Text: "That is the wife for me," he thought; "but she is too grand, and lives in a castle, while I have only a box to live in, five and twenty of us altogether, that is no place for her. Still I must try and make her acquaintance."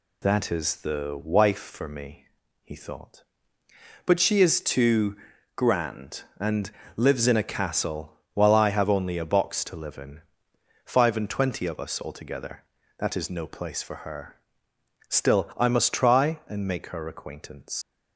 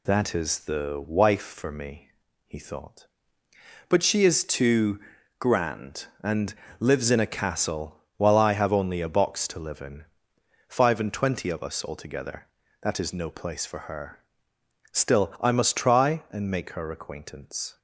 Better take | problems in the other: second | pauses between "too" and "grand"; at 5.1 s; 0.40 s long; also in the second // pauses between "and" and "lives"; slight; at 6.7 s; 0.24 s long; slight in the second // leaves "acquaintance" unfinished; at 17.8 s; 130 ms

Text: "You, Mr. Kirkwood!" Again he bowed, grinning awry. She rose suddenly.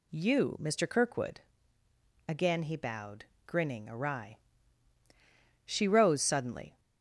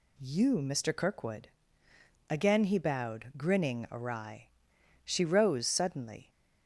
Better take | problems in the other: neither | none

